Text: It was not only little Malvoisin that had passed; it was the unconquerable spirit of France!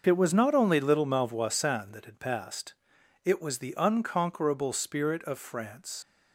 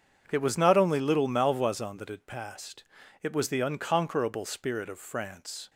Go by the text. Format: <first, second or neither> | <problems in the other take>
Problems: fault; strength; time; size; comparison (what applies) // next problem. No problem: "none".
second | starts louder than the rest; noticeable; until 1.0 s; 6 dB // leaves "France" unfinished; at 6.0 s; 105 ms